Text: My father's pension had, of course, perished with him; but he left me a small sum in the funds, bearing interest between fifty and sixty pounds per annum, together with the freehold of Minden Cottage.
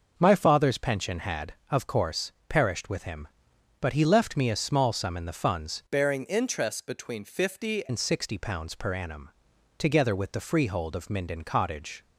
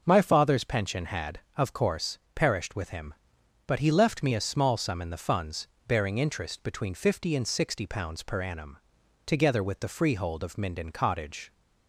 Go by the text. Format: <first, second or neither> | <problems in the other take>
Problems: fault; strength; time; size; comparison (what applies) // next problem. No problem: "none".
second | changes voice from "bearing" to "fifty"; from 5.8 to 7.8 s; 2.0 s long